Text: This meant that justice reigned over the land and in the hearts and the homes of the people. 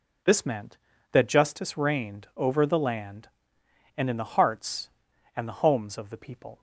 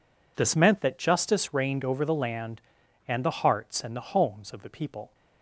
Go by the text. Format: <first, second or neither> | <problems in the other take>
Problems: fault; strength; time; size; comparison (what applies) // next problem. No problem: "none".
first | skips "in"; at 3.2 s